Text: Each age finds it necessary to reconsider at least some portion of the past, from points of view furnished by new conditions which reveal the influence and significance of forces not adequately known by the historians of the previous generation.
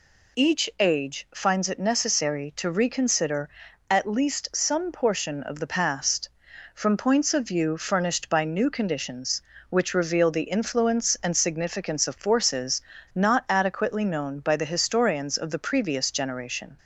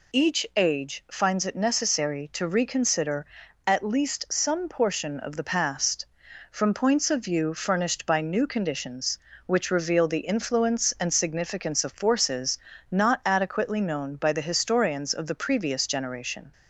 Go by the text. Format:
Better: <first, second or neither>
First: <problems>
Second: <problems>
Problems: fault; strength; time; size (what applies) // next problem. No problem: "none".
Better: neither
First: pauses between "forces" and "not"; slight; at 12.8 s; 0.32 s long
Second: pauses between "forces" and "not"; slight; at 12.5 s; 0.32 s long